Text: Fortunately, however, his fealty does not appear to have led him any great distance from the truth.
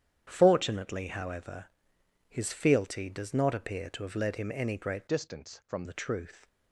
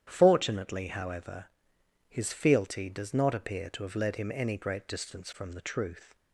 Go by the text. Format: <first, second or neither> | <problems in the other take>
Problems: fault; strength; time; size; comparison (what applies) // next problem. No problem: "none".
second | starts louder than the rest; strong; until 1.3 s; 9.5 dB; strong in the second // changes voice from "distance" to "from"; from 5.0 to 5.8 s; 0.8 s long